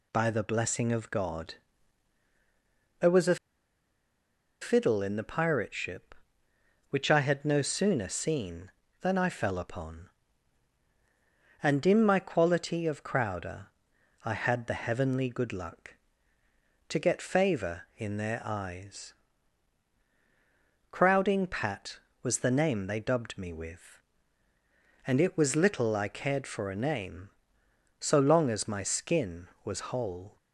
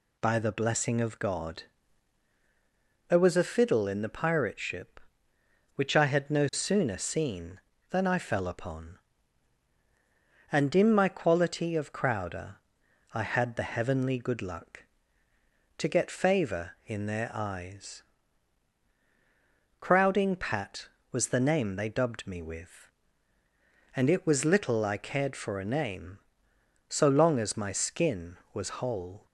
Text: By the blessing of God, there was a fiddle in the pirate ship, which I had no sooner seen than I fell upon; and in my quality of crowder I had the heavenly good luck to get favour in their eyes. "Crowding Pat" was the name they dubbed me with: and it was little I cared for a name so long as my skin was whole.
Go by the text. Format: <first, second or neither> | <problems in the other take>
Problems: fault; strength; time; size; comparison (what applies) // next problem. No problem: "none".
second | pauses between "a" and "fiddle"; strong; at 3.3 s; 1.2 s long // pauses between "crowder" and "I"; noticeable; at 13.6 s; 0.58 s long; noticeable in the second